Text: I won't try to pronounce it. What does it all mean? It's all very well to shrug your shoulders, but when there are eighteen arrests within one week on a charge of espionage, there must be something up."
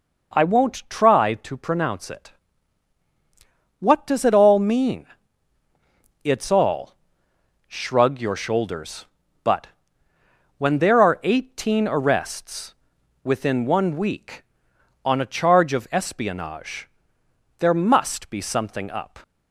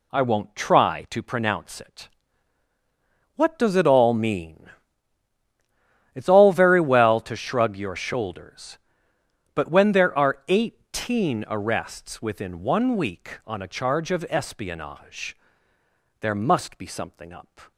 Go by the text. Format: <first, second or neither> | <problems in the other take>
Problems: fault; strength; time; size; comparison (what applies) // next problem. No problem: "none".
second | skips "very well to"; at 7.3 s // pauses between "but" and "when"; noticeable; at 9.6 s; 0.88 s long // pauses between "arrests" and "within"; noticeable; at 12.7 s; 0.50 s long